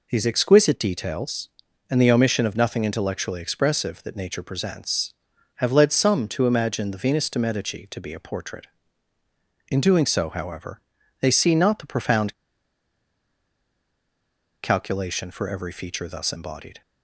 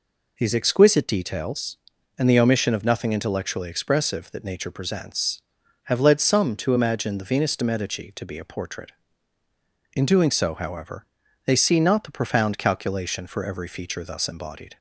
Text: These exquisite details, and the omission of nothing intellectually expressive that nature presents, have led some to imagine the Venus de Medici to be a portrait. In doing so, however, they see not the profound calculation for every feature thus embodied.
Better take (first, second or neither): second